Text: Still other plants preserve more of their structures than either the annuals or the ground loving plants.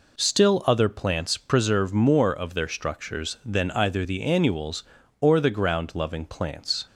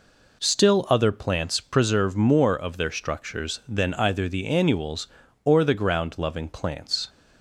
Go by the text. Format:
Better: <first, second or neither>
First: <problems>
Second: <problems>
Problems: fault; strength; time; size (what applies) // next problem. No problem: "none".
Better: neither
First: none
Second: none